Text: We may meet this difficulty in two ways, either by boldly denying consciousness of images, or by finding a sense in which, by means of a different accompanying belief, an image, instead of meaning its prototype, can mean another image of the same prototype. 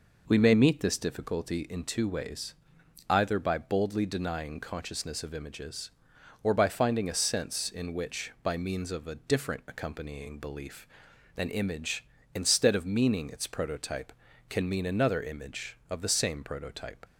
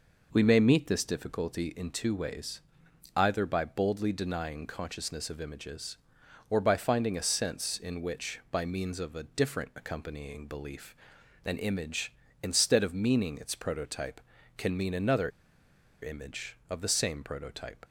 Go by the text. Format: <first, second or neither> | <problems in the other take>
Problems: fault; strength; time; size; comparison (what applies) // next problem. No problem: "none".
first | pauses between "another" and "image"; noticeable; at 15.2 s; 0.73 s long